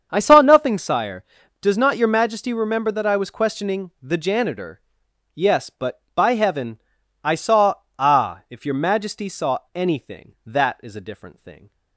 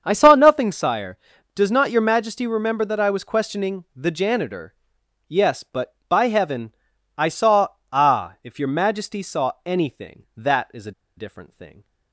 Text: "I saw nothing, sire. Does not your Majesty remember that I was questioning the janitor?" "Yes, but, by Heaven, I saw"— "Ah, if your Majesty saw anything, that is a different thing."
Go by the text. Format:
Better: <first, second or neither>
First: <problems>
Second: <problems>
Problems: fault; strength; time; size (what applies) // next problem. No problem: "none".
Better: first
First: starts louder than the rest; strong; until 1.1 s; 7 dB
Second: starts louder than the rest; strong; until 1.0 s; 7 dB // pauses between "a" and "different"; slight; at 10.9 s; 0.25 s long